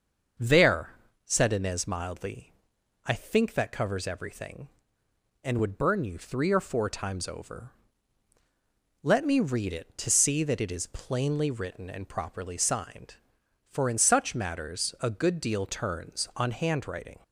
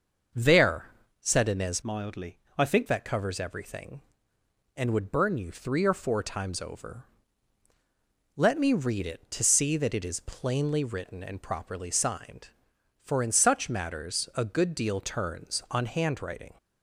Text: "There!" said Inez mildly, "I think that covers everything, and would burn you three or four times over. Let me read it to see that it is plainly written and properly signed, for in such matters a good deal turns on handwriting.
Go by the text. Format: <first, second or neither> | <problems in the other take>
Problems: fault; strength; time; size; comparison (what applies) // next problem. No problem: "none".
first | starts louder than the rest; until 1.6 s; 6.5 dB; also in the first // changes voice from "mildly" to "think"; from 1.8 to 2.8 s; 1.0 s long